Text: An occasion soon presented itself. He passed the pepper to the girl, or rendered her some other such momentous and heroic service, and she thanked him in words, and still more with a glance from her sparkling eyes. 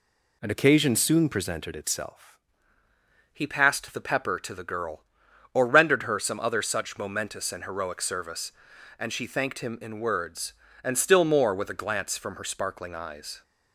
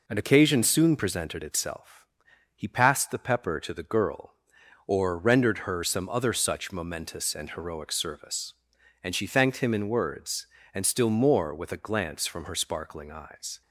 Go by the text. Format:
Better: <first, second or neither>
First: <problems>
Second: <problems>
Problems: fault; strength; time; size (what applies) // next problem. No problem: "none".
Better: second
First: changes voice at "He"; from 3.3 s on; 10.1 s long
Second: none